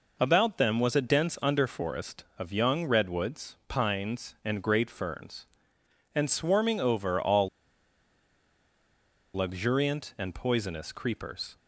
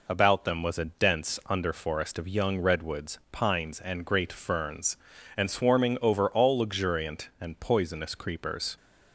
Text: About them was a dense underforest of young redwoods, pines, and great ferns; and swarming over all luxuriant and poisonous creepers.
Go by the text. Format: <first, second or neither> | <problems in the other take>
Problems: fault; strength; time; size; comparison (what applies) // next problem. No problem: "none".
second | pauses between "all" and "luxuriant"; strong; at 7.4 s; 1.8 s long